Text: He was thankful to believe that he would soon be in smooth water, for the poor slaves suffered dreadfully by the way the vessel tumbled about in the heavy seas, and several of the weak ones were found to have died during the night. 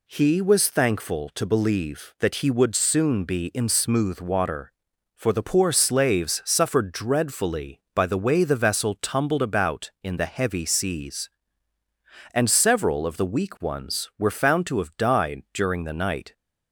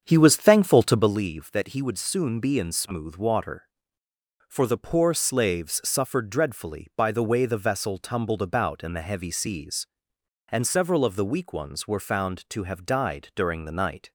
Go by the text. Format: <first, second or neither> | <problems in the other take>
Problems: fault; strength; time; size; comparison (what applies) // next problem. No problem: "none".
first | starts louder than the rest; strong; until 1.2 s; 7.5 dB